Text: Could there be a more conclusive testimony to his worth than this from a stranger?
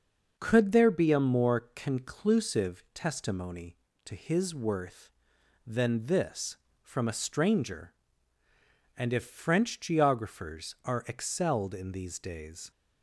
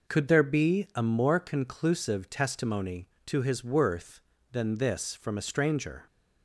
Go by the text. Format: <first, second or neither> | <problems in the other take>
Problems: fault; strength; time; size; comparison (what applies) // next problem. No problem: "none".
second | starts louder than the rest; noticeable; until 1.3 s; 6 dB // goes on to say "and if French geographers are excelled in these days"; strong; from 8.9 s on; 3.7 s long